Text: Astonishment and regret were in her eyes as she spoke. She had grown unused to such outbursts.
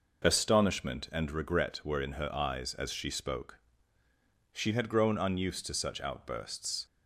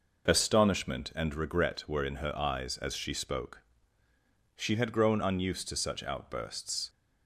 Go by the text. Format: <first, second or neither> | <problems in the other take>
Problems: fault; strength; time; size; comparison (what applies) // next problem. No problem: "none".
neither | none